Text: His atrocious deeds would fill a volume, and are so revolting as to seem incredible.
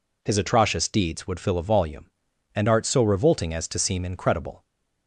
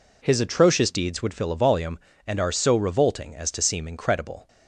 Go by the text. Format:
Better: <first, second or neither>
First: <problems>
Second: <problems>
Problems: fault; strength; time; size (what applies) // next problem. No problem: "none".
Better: second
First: says "art" for "are"; at 2.6 s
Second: none